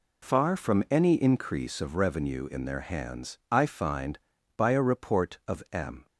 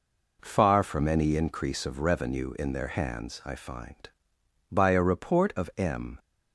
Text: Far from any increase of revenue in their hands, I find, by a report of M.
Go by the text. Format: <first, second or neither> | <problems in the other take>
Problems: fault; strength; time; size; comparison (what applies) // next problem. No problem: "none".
neither | none